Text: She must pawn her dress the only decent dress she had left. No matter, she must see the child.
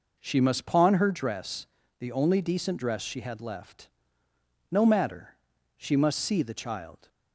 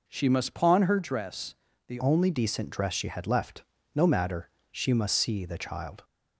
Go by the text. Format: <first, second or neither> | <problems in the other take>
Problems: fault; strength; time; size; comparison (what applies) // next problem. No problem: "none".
first | pauses between "dress" and "the"; slight; at 1.5 s; 0.34 s long; slight in the first // changes voice at "only"; from 1.9 s on; 4.1 s long